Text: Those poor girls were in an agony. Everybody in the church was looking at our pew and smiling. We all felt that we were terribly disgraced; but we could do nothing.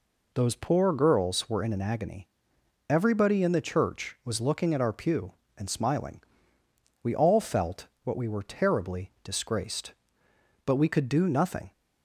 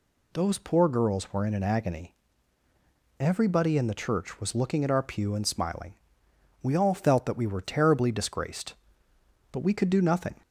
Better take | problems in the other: second | says "what" for "that"; at 8.0 s

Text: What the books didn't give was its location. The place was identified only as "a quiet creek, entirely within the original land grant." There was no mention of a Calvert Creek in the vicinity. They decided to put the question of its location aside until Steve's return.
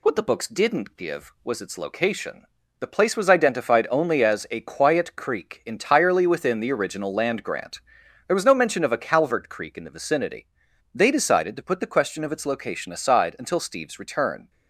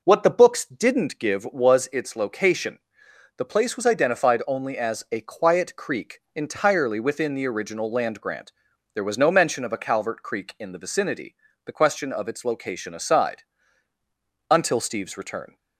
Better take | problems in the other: first | skips "They decided to put"; at 11.5 s // pauses between "aside" and "until"; at 13.4 s; 1.0 s long

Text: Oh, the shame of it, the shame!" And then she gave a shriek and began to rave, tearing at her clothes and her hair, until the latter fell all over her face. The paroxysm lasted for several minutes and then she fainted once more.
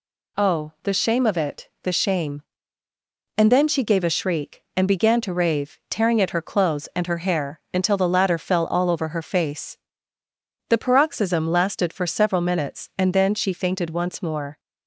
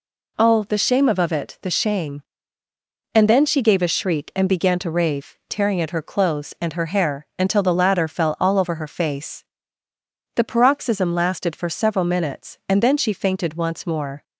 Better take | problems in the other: first | says "of" twice; at 1.1 s

